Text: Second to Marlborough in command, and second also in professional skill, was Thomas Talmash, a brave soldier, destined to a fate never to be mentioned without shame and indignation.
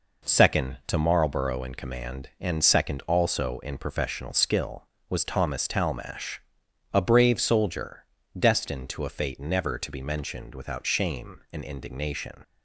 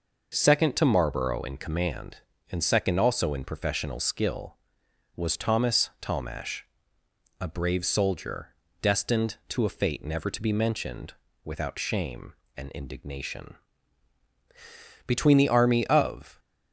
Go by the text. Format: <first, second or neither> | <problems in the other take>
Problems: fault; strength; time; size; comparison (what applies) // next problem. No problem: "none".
first | pauses between "mentioned" and "without"; slight; at 11.1 s; 0.32 s long // goes on to say "Between the army of"; from 15.0 s on; 1.3 s long